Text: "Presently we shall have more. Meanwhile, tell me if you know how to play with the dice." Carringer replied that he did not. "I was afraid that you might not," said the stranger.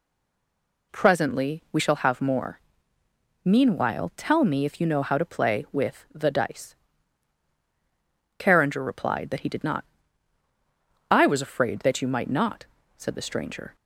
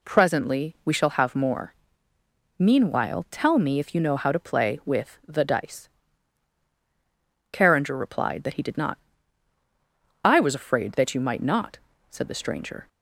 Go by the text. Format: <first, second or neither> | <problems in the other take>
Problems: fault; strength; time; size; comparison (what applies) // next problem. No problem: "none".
second | stays silent before the first word; slight; until 0.9 s; 0.9 s long